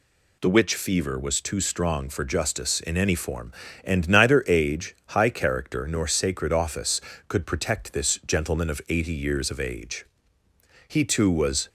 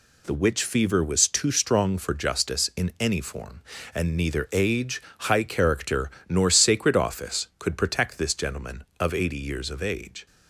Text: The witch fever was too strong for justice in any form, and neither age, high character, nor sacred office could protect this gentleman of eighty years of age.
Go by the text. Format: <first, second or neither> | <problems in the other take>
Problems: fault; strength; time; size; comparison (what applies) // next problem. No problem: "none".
second | goes on to say "He too was"; noticeable; from 10.8 s on; 0.82 s long